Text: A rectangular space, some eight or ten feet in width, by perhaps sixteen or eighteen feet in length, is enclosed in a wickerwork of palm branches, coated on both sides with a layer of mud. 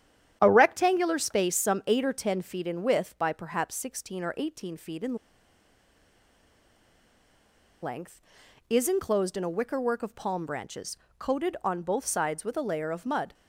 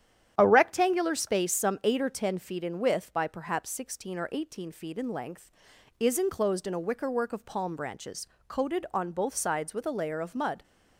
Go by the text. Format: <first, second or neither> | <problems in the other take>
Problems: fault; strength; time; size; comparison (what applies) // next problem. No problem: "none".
second | starts louder than the rest; strong; until 1.4 s; 10 dB; strong in the second // pauses between "in" and "length"; strong; at 5.1 s; 2.6 s long